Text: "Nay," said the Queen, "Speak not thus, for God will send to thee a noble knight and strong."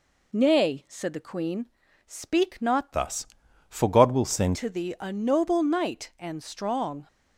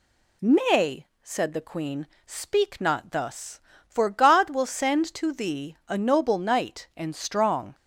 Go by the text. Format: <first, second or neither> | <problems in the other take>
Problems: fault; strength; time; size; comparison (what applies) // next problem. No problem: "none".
second | changes voice from "thus" to "send"; from 2.9 to 4.5 s; 1.6 s long